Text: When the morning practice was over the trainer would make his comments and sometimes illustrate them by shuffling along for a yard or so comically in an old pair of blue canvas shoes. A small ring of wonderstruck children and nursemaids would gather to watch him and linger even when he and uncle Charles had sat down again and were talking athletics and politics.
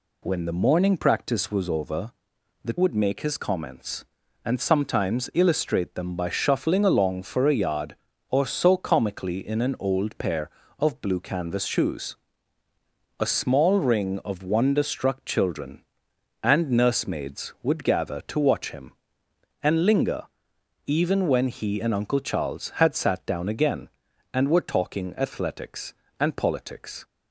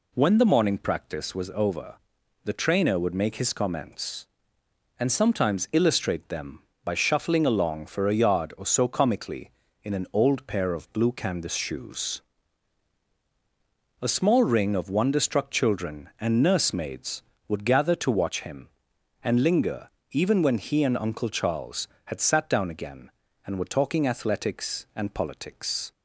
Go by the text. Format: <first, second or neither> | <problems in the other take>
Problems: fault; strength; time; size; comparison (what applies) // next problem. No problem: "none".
second | pauses between "over" and "the"; noticeable; at 2.1 s; 0.52 s long; noticeable in the second // skips "trainer"; at 2.7 s // pauses between "linger" and "even"; noticeable; at 20.2 s; 0.64 s long; slight in the second